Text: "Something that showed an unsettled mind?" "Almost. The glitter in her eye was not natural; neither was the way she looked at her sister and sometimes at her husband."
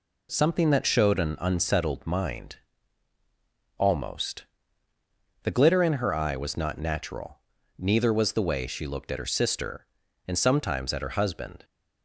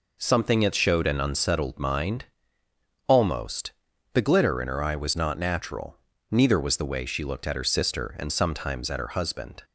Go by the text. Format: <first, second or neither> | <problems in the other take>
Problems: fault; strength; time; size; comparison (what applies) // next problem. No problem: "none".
neither | none